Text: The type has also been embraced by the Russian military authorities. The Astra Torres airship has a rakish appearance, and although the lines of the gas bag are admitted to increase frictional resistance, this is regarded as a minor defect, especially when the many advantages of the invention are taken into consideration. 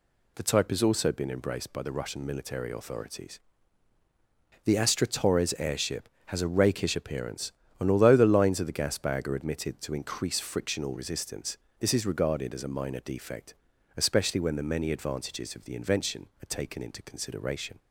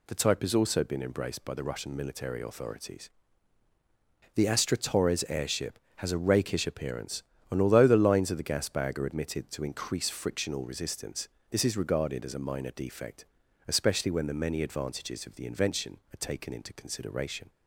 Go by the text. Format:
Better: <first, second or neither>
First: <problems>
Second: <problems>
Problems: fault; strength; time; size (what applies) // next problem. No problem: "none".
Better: neither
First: none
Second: none